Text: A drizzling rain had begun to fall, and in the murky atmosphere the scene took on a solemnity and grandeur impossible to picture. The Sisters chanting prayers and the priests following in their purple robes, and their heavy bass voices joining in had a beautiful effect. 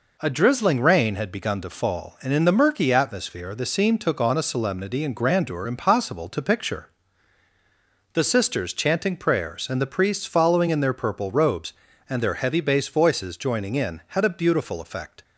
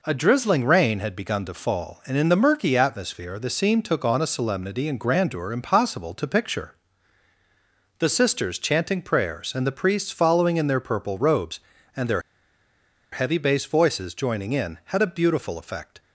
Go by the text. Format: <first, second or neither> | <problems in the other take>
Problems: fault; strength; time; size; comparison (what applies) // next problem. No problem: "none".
first | pauses between "their" and "heavy"; noticeable; at 12.2 s; 0.91 s long